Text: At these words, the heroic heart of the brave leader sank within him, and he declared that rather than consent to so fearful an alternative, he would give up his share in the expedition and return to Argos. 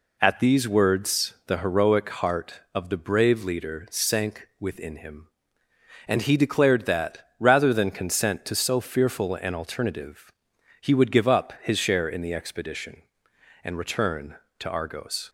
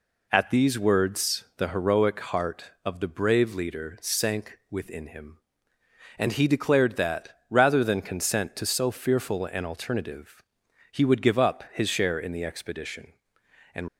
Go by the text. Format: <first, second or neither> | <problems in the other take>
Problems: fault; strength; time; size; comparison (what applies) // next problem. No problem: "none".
first | pauses between "that" and "rather"; slight; at 7.2 s; 0.18 s long; slight in the first // stops before "return to Argos"; at 13.8 s